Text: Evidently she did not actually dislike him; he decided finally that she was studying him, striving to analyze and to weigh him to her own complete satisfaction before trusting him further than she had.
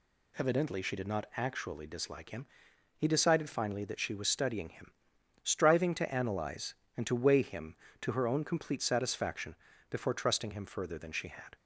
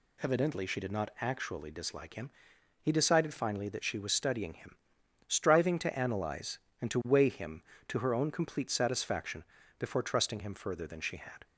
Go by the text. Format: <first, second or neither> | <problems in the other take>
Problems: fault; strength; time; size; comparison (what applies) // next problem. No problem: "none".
neither | pauses between "satisfaction" and "before"; slight; the same in both